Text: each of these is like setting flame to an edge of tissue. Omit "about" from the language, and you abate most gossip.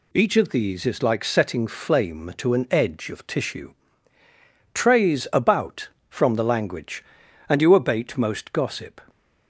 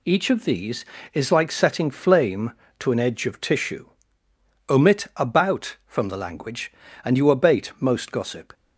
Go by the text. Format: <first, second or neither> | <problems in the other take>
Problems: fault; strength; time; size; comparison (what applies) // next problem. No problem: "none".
second | says "Trays" for "Omit"; at 4.7 s